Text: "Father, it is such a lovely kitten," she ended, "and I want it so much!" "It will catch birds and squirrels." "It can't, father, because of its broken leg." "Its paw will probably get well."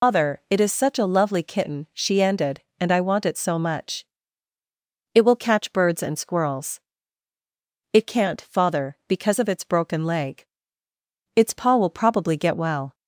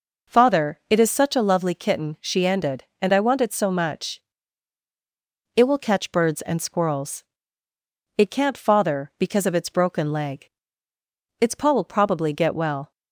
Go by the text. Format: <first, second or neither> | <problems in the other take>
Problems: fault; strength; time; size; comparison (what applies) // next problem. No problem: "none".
second | loses the start of "Father"; at 0.0 s; 175 ms